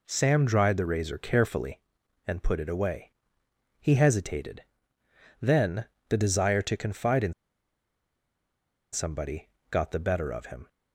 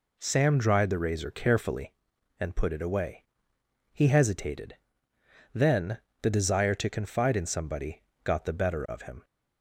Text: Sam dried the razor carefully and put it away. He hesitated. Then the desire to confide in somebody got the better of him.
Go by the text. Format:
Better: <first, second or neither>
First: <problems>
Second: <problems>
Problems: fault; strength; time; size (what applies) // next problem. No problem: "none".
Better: second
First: pauses between "Then" and "the"; slight; at 5.8 s; 0.22 s long // pauses between "in" and "somebody"; strong; at 7.3 s; 1.5 s long // pauses between "somebody" and "got"; slight; at 9.4 s; 0.22 s long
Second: pauses between "Then" and "the"; slight; at 5.9 s; 0.22 s long // pauses between "somebody" and "got"; slight; at 8.0 s; 0.22 s long